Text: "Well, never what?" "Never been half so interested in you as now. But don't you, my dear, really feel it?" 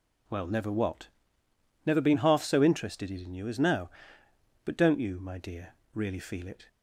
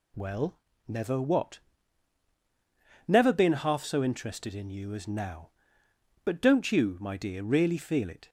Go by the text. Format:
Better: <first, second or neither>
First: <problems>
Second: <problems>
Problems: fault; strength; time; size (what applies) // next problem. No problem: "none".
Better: neither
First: none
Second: none